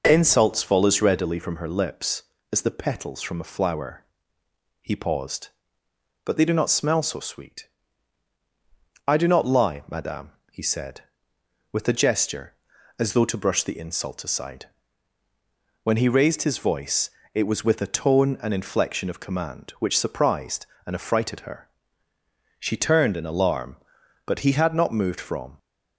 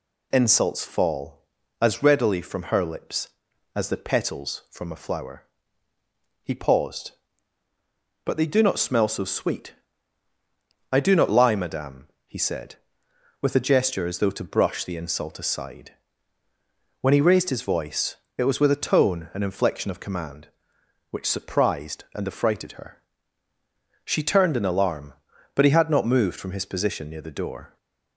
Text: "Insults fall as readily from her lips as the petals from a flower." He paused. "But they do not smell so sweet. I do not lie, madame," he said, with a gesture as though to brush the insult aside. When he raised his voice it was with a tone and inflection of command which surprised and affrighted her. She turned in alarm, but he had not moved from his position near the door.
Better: second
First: pauses between "voice" and "it"; slight; at 17.0 s; 0.24 s long // stops before "his position near the door"; at 25.5 s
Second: pauses between "voice" and "it"; slight; at 18.1 s; 0.22 s long

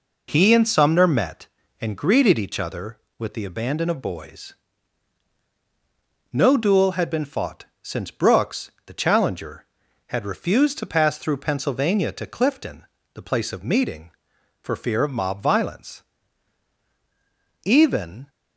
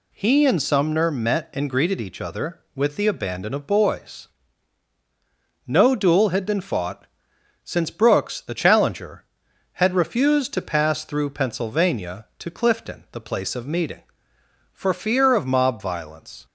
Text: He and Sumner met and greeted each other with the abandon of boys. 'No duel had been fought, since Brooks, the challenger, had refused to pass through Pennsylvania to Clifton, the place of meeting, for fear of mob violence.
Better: second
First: goes on to say "Even"; noticeable; from 17.6 s on; 0.66 s long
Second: none

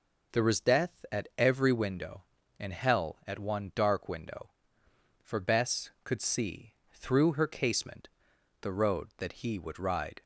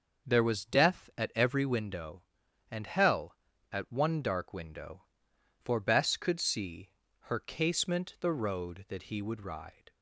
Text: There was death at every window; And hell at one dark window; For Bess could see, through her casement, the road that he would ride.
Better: first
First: none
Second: starts louder than the rest; noticeable; until 1.3 s; 6 dB // skips "through"; at 7.0 s

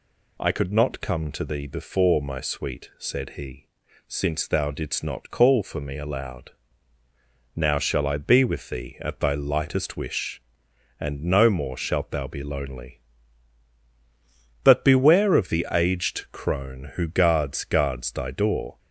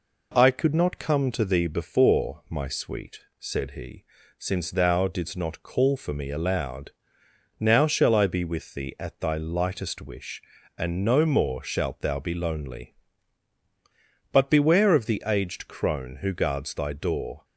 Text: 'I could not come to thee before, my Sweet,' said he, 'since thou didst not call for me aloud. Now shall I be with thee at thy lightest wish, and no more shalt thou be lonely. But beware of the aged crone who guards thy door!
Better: second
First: says "guards" twice; at 17.6 s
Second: none

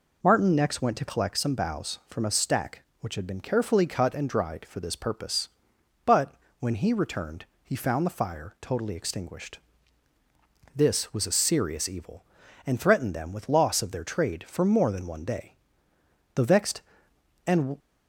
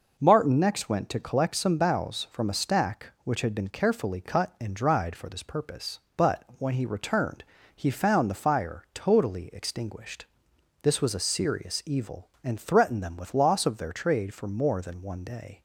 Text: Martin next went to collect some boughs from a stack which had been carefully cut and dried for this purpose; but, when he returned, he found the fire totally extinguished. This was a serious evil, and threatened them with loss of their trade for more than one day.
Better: second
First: goes on to say "The vexed and"; from 16.3 s on; 1.4 s long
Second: none

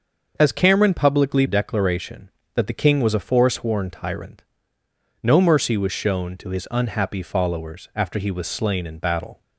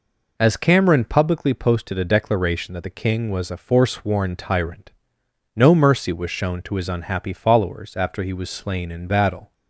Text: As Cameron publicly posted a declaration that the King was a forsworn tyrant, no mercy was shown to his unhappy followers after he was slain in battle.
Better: second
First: starts louder than the rest; until 1.3 s; 6.5 dB // skips "posted a"; at 1.4 s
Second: none

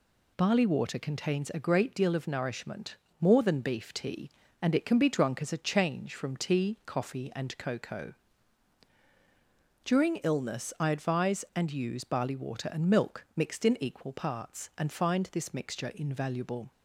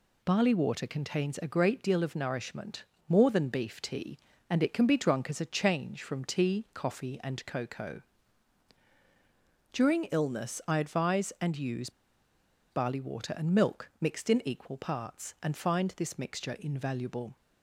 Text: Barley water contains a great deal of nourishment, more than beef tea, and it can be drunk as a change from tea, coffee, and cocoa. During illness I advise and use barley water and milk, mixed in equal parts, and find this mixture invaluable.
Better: first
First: none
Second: pauses between "use" and "barley"; noticeable; at 11.8 s; 0.81 s long

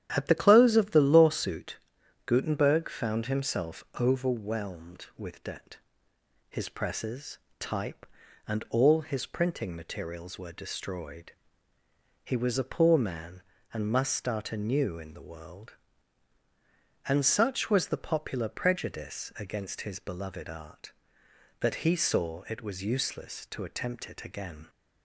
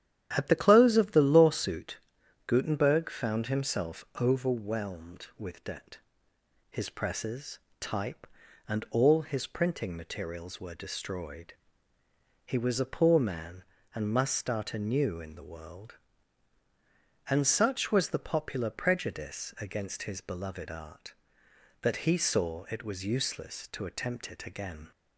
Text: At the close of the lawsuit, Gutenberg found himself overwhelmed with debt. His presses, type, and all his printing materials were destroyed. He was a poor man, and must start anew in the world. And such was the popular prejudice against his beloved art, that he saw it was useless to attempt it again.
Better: neither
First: starts louder than the rest; strong; until 1.1 s; 10.5 dB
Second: starts louder than the rest; strong; until 1.3 s; 11 dB

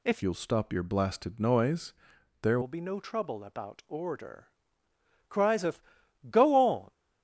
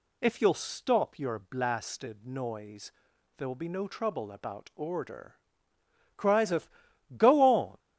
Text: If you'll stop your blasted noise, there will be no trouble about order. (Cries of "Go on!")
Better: second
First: changes voice from "you'll" to "there"; from 0.2 to 2.6 s; 2.4 s long // pauses between "of" and "Go"; noticeable; at 5.8 s; 0.48 s long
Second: pauses between "of" and "Go"; noticeable; at 6.6 s; 0.47 s long

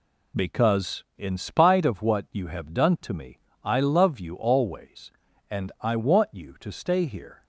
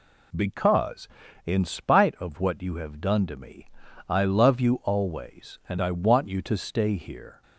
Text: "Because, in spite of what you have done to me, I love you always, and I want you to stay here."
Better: neither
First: none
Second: none

